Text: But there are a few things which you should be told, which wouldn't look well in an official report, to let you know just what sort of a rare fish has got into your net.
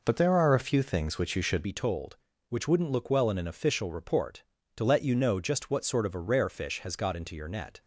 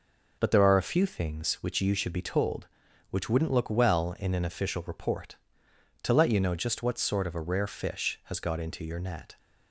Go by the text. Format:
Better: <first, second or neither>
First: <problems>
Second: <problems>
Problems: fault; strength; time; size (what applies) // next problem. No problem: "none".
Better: second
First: changes voice at "be"; from 1.6 s on; 6.2 s long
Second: none